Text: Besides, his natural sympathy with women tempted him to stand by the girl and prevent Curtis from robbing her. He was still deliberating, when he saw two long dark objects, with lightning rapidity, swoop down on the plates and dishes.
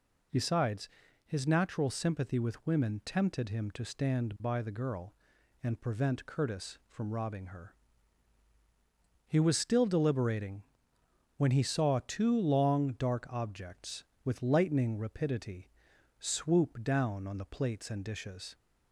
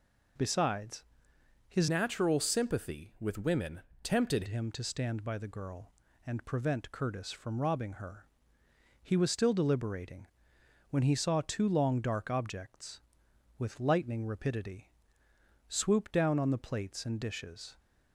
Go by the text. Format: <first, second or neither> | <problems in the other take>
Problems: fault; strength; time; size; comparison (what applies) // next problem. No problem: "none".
first | changes voice from "natural" to "tempted"; from 1.8 to 4.4 s; 2.6 s long // pauses between "women" and "tempted"; slight; at 3.8 s; 0.22 s long